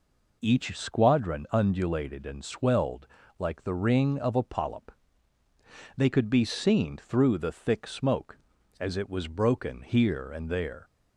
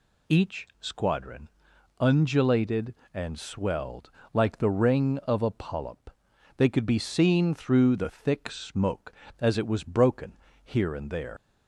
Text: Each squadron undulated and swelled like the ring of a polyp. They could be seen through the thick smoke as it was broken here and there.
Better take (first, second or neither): first